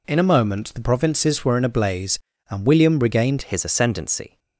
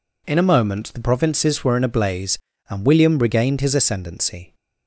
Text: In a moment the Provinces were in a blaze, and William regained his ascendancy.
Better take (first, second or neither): second